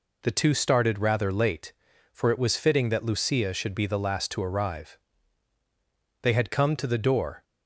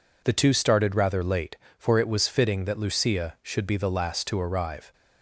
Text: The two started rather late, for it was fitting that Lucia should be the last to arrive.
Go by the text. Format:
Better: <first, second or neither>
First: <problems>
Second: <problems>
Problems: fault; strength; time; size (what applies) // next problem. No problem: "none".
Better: second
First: goes on to say "They had come to the door"; noticeable; from 6.2 s on; 1.2 s long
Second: none